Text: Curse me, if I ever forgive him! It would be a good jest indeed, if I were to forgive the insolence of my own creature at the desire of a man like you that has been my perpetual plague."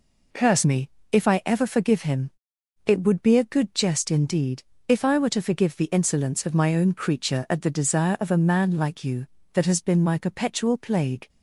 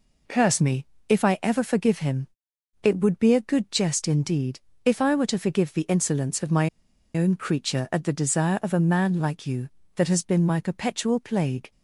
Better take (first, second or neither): first